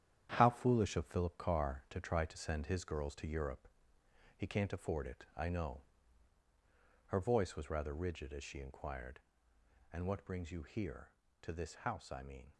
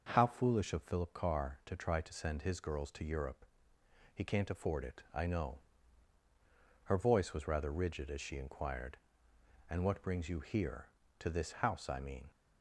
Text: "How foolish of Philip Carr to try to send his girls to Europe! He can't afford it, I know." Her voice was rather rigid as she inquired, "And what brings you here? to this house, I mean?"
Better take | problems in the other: second | gets quieter; strong; throughout; 8.5 dB

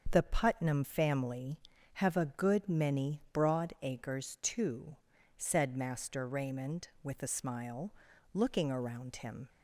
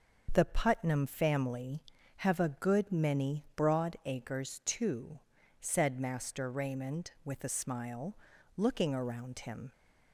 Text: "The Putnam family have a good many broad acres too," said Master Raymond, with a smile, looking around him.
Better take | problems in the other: neither | starts louder than the rest; the same in both

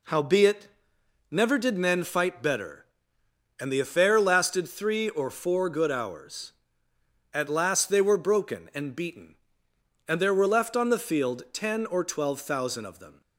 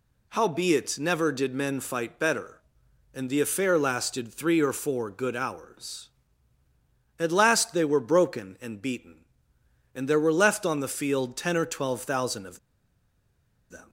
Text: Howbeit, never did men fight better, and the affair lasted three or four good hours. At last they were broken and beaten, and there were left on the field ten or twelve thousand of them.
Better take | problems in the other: first | pauses between "of" and "them"; at 12.5 s; 1.1 s long

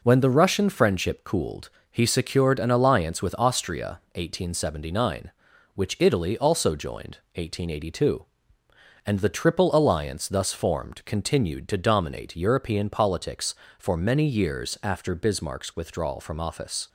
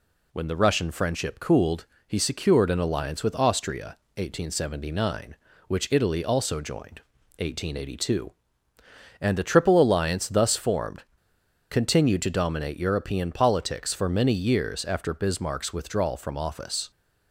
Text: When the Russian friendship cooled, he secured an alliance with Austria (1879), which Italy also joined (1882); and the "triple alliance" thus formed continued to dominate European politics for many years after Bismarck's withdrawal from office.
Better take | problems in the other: first | pauses between "formed" and "continued"; noticeable; at 11.0 s; 0.68 s long

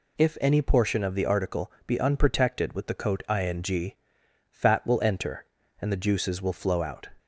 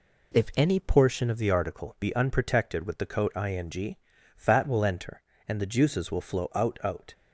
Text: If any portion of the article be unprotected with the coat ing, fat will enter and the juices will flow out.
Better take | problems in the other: first | says "out" twice; at 6.8 s

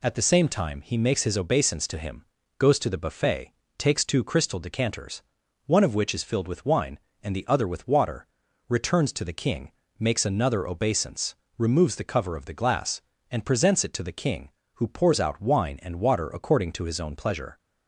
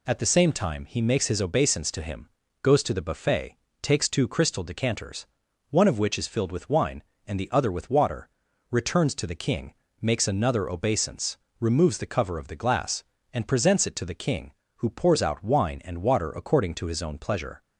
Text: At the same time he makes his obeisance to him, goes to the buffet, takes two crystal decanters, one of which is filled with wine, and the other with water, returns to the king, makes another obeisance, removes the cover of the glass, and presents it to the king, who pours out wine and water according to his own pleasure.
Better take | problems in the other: neither | none

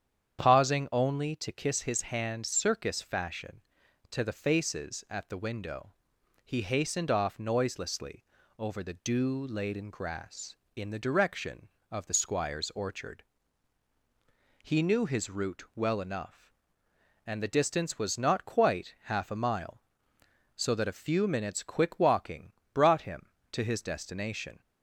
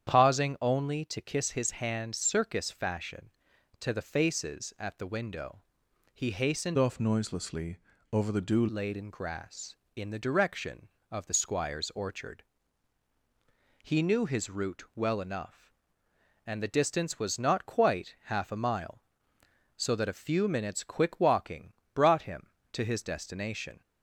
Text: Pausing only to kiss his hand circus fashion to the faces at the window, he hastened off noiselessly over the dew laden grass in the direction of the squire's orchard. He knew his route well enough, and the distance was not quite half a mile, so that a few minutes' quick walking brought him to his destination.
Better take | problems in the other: first | starts louder than the rest; strong; until 1.1 s; 9 dB; strong in the first // changes voice from "off" to "dew"; from 6.7 to 8.6 s; 1.9 s long // pauses between "noiselessly" and "over"; slight; at 7.7 s; 0.36 s long; slight in the first // pauses between "walking" and "brought"; slight; at 21.7 s; 0.22 s long; slight in the first

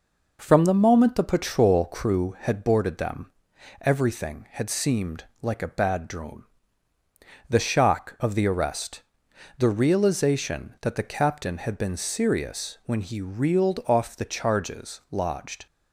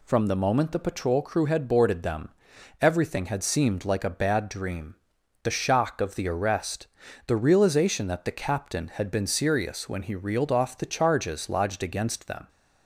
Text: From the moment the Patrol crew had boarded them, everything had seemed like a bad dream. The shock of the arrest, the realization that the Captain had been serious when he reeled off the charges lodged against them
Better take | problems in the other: second | pauses between "seemed" and "like"; slight; at 5.2 s; 0.18 s long // stops before "against them"; at 15.6 s

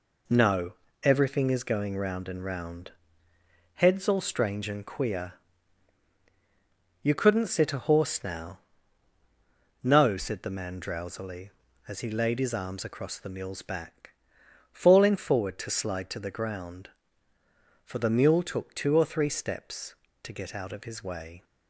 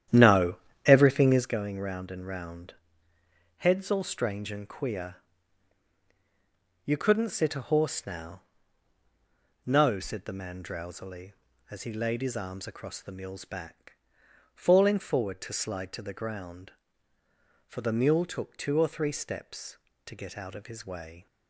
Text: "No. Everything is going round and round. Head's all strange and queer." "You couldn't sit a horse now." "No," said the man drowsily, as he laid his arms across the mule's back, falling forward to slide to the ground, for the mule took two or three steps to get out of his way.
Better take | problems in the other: first | starts louder than the rest; strong; until 1.6 s; 10.5 dB

